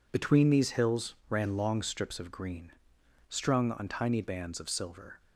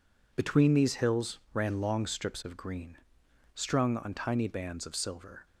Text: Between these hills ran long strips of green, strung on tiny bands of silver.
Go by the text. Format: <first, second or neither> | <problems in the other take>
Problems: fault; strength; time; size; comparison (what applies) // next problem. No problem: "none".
neither | none